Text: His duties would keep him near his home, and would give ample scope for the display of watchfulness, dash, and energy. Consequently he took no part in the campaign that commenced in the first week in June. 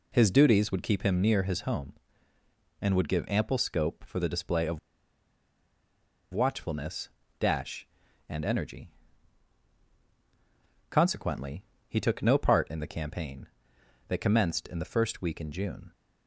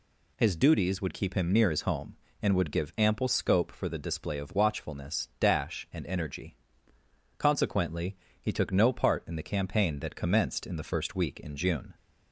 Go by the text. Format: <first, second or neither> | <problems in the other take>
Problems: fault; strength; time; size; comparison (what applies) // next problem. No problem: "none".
second | pauses between "of" and "watchfulness"; strong; at 4.7 s; 1.5 s long // pauses between "Consequently" and "he"; slight; at 11.6 s; 0.22 s long; slight in the second